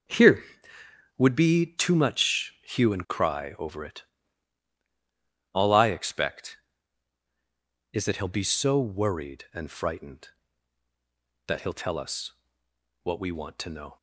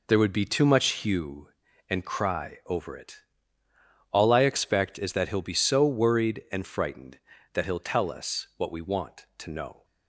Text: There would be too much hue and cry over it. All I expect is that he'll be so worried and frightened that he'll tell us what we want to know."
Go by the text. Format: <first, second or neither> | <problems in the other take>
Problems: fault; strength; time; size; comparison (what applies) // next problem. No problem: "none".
second | says "Here" for "There"; at 0.0 s // pauses between "us" and "what"; noticeable; at 12.3 s; 0.70 s long